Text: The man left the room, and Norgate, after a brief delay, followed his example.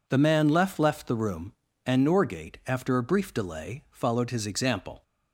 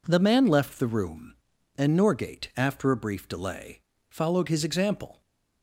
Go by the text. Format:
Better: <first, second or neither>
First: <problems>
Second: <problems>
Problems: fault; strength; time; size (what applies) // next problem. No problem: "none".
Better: second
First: says "left" twice; at 0.7 s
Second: none